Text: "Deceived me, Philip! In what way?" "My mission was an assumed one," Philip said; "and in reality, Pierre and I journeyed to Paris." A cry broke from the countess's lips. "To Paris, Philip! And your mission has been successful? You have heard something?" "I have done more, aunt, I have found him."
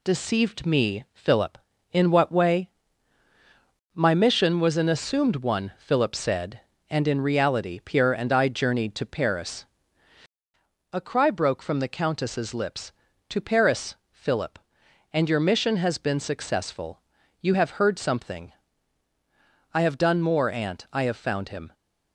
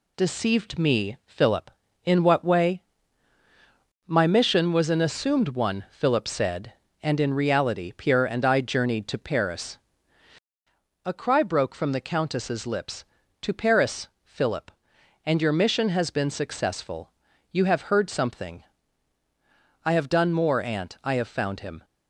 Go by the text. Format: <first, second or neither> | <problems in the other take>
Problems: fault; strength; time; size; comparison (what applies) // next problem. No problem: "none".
neither | none